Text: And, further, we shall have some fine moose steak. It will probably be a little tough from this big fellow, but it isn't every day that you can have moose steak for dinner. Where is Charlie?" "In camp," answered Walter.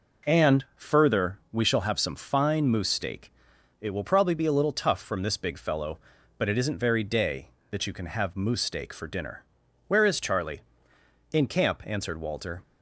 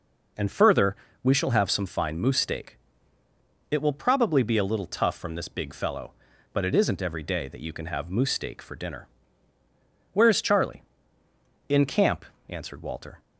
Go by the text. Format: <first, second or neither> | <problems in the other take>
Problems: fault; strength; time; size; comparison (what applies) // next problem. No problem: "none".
second | says "very" for "every"; at 6.7 s